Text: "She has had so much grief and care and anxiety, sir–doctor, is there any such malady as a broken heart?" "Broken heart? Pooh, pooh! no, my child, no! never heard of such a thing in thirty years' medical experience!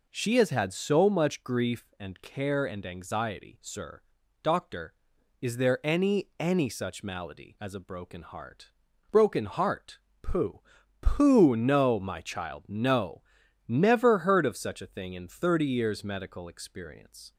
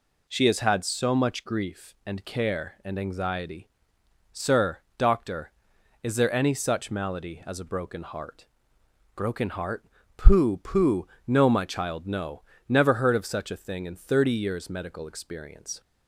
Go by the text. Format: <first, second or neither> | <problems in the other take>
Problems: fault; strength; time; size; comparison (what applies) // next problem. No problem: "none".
second | says "any" twice; at 6.3 s